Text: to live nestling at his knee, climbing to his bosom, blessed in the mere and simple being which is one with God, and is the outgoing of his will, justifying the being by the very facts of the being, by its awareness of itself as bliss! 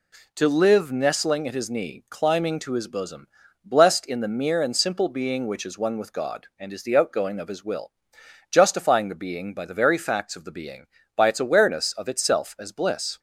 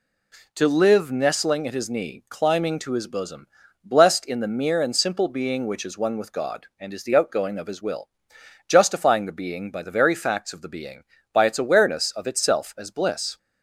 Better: neither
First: none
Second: none

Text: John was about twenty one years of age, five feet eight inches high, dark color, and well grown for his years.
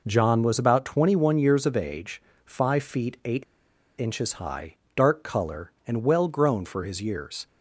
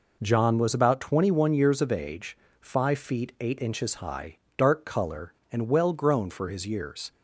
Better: second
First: pauses between "eight" and "inches"; noticeable; at 3.4 s; 0.56 s long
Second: none

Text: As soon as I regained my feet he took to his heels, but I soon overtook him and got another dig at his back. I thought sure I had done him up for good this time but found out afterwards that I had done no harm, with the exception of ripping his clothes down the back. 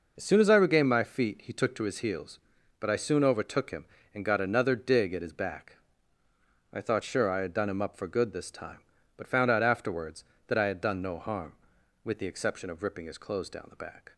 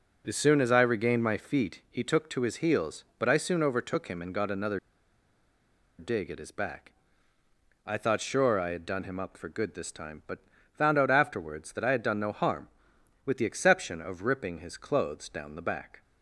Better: first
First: none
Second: pauses between "another" and "dig"; at 4.7 s; 1.1 s long // pauses between "but" and "found"; slight; at 10.3 s; 0.34 s long

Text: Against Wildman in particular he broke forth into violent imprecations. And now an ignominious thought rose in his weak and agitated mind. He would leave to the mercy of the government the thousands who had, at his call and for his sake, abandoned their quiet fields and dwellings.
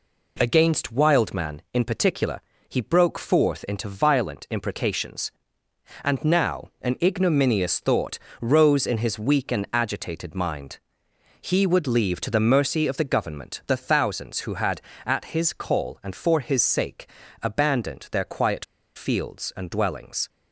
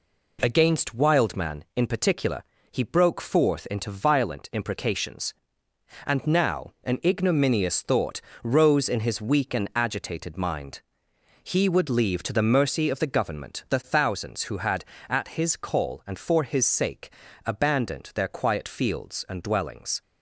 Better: second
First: pauses between "particular" and "he"; slight; at 2.4 s; 0.28 s long // pauses between "thought" and "rose"; slight; at 8.1 s; 0.20 s long // pauses between "quiet" and "fields"; slight; at 18.6 s; 0.31 s long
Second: pauses between "particular" and "he"; slight; at 2.4 s; 0.28 s long // pauses between "thought" and "rose"; slight; at 8.2 s; 0.20 s long

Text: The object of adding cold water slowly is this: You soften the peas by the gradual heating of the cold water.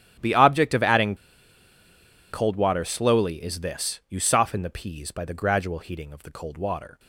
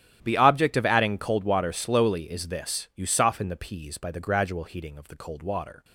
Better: second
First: starts louder than the rest; strong; until 2.3 s; 12 dB // pauses between "adding" and "cold"; at 1.1 s; 1.1 s long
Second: starts louder than the rest; strong; until 1.2 s; 11.5 dB

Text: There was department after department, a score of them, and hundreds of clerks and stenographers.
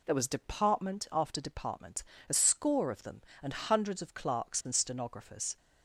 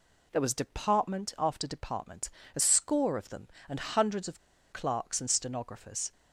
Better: first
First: none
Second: pauses between "of" and "clerks"; slight; at 4.3 s; 0.33 s long

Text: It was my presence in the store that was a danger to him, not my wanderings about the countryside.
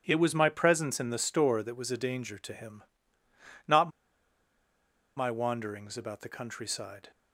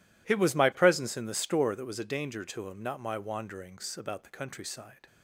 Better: second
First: pauses between "not" and "my"; strong; at 3.8 s; 1.2 s long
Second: none

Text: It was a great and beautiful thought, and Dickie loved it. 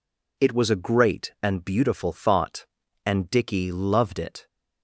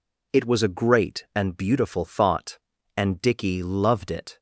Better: neither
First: none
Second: none

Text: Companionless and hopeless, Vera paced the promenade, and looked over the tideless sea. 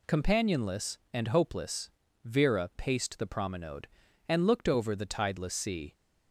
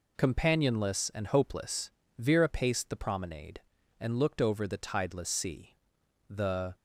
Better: first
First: none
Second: goes on to say "The"; slight; from 6.2 s on; 0.46 s long

